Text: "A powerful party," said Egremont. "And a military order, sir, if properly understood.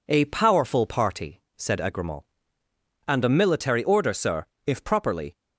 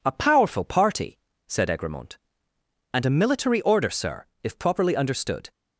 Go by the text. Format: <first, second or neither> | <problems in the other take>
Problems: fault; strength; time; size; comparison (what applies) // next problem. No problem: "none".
second | stops before "understood"; at 5.3 s